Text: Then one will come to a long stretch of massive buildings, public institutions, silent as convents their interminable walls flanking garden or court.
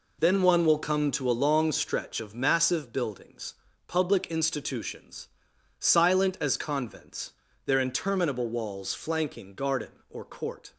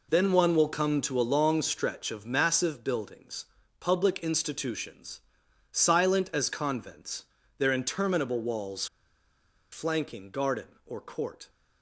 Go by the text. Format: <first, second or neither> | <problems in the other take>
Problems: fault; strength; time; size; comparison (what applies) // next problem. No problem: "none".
first | pauses between "convents" and "their"; slight; at 7.2 s; 0.36 s long; slight in the first // pauses between "walls" and "flanking"; noticeable; at 8.8 s; 0.86 s long